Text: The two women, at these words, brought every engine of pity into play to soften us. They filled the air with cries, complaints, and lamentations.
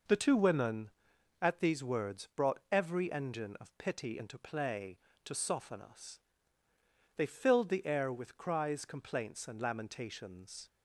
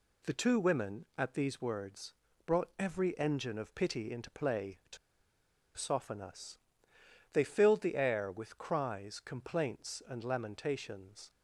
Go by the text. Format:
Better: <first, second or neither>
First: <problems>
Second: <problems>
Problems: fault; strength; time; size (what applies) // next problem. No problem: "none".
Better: first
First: none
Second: pauses between "to" and "soften"; noticeable; at 4.9 s; 0.80 s long